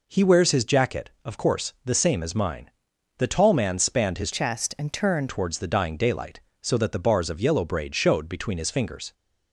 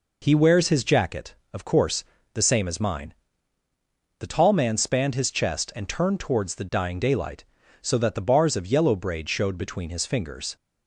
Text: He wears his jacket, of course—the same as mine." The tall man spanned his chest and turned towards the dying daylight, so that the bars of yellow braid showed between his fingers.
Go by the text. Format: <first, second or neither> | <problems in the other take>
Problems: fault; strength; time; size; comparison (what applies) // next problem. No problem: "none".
second | changes voice from "chest" to "turned"; from 4.3 to 5.2 s; 0.9 s long